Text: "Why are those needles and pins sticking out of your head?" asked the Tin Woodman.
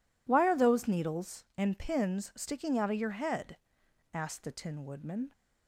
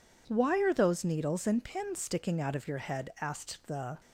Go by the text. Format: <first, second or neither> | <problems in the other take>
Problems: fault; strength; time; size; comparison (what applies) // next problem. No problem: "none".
first | stops before "Tin Woodman"; at 3.9 s